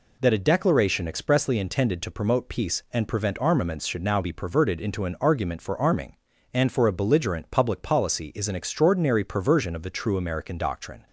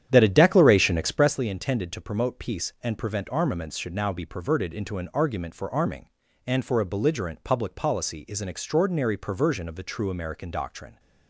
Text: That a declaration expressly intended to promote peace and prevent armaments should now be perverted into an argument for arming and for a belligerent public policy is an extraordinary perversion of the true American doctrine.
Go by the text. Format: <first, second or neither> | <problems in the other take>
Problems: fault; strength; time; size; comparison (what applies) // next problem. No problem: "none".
first | starts louder than the rest; strong; until 1.4 s; 10 dB